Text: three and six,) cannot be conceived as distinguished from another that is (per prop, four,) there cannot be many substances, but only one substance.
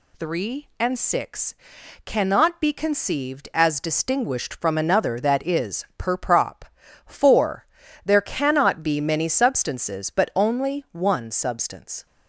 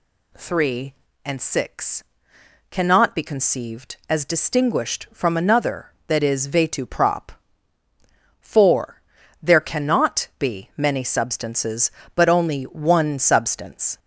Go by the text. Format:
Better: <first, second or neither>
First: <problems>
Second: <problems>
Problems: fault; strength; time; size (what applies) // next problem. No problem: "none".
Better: first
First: none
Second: says "vetu" for "per"; at 6.4 s